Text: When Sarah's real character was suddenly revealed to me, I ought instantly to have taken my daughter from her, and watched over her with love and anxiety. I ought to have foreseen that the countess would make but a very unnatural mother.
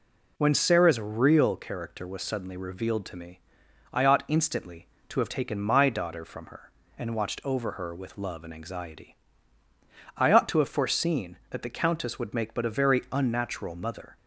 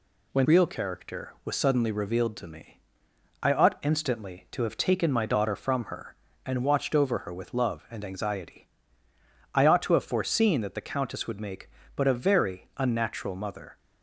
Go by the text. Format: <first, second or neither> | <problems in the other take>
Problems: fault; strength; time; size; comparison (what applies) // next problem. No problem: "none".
first | skips "Sarah's"; at 0.4 s